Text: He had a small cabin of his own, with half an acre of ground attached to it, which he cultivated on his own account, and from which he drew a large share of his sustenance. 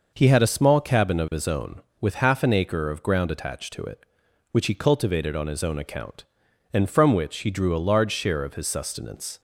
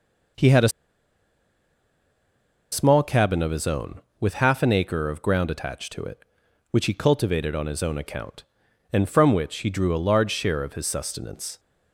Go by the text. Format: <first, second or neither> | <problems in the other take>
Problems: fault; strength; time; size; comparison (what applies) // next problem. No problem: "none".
first | pauses between "a" and "small"; strong; at 0.6 s; 2.0 s long